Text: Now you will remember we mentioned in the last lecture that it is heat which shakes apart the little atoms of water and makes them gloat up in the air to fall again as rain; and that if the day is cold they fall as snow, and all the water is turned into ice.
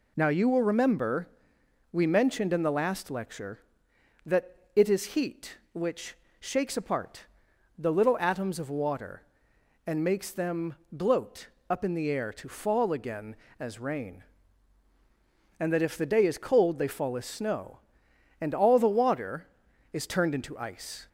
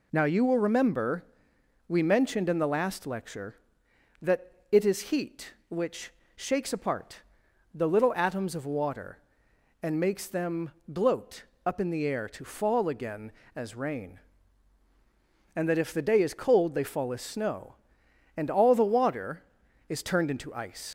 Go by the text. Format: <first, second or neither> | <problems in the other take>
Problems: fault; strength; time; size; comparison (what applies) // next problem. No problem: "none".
first | pauses between "remember" and "we"; noticeable; at 1.2 s; 0.64 s long; noticeable in the first // pauses between "that" and "it"; slight; at 4.5 s; 0.18 s long; slight in the first // pauses between "which" and "shakes"; slight; at 6.1 s; 0.24 s long; slight in the first // pauses between "apart" and "the"; noticeable; at 7.2 s; 0.52 s long; noticeable in the first // pauses between "them" and "gloat"; slight; at 10.6 s; 0.22 s long; slight in the first // pauses between "gloat" and "up"; slight; at 11.4 s; 0.22 s long; slight in the first // leaves "ice" unfinished; at 20.8 s; 110 ms